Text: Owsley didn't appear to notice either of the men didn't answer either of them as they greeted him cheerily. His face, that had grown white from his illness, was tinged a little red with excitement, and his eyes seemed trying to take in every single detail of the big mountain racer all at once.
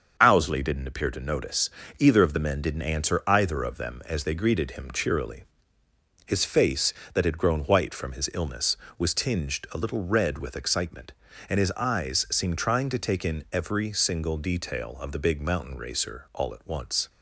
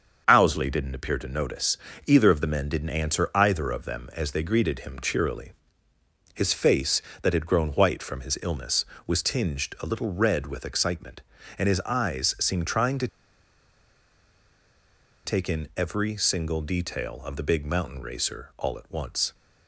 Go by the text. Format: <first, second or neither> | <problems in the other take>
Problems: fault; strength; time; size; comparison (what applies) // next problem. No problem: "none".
first | starts louder than the rest; until 1.2 s; 7 dB; also in the first // pauses between "notice" and "either"; slight; at 1.7 s; 0.30 s long; slight in the first // pauses between "to" and "take"; strong; at 13.0 s; 2.1 s long